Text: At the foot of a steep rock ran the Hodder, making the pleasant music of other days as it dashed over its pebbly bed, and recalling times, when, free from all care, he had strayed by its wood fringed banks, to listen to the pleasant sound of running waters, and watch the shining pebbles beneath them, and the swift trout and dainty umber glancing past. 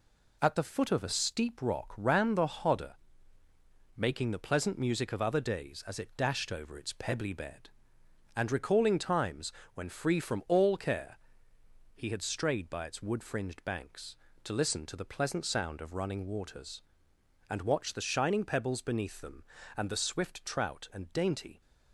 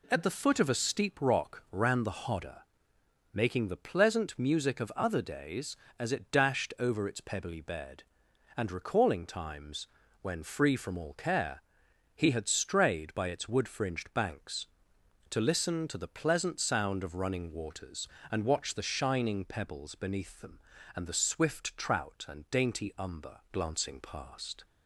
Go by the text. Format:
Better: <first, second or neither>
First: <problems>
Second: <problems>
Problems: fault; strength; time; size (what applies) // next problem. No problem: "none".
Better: second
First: stops before "umber glancing past"; at 21.6 s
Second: none